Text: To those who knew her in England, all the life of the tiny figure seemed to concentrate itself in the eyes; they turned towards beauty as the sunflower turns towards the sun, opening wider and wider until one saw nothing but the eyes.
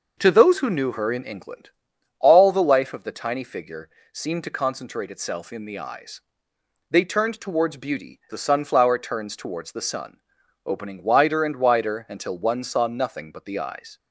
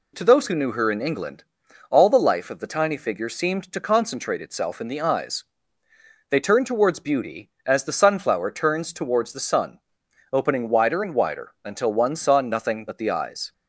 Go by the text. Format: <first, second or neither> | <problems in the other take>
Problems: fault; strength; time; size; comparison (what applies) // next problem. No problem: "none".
second | pauses between "figure" and "seemed"; slight; at 3.8 s; 0.22 s long // skips "as"; at 8.2 s